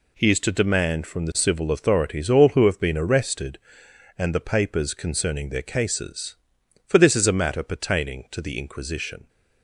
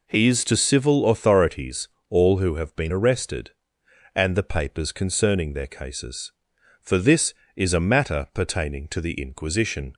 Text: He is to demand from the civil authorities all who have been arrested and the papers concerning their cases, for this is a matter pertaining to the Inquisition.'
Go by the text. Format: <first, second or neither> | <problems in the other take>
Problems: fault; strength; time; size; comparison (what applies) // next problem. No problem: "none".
first | skips "demand from the"; at 0.5 s // pauses between "authorities" and "all"; slight; at 1.8 s; 0.20 s long